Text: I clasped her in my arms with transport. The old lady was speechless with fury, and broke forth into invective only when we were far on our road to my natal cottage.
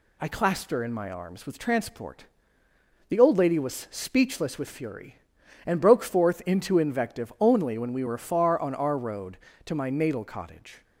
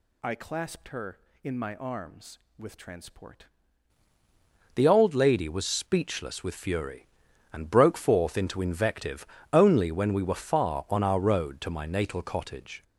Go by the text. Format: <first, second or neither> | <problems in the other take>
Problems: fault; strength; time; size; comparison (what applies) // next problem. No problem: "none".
first | changes voice at "The"; from 4.7 s on; 8.1 s long // pauses between "invective" and "only"; slight; at 9.2 s; 0.28 s long